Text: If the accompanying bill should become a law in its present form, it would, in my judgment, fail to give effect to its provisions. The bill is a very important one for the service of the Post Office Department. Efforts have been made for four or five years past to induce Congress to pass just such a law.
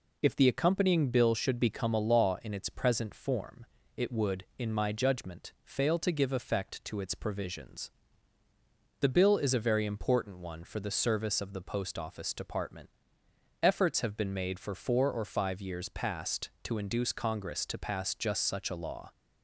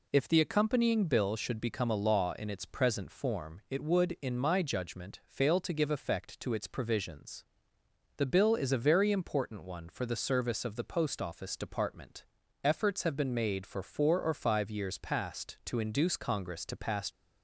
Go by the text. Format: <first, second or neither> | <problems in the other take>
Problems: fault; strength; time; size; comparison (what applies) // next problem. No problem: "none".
first | stops before "just such a law"; at 17.0 s